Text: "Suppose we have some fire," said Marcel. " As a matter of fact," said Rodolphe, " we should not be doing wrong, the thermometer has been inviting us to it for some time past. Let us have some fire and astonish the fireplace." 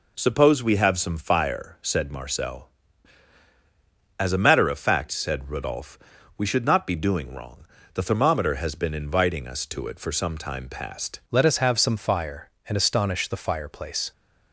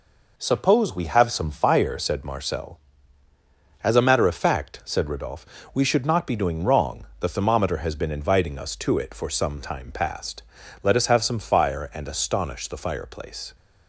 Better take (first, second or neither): second